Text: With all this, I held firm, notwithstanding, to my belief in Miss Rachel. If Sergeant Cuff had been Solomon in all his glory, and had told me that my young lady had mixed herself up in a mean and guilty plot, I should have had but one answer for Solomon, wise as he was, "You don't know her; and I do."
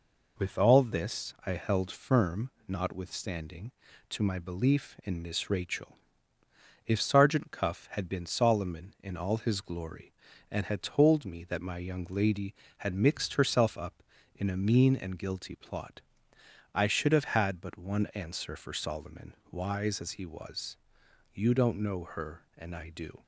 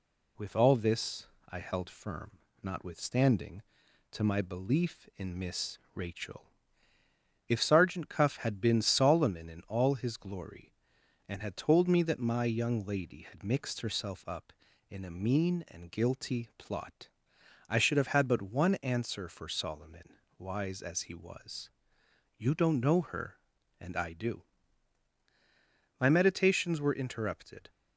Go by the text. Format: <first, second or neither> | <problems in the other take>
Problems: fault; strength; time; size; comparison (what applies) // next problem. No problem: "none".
first | pauses between "Miss" and "Rachel"; slight; at 5.7 s; 0.16 s long // goes on to say "My meditations were interrupted"; strong; from 25.9 s on; 1.7 s long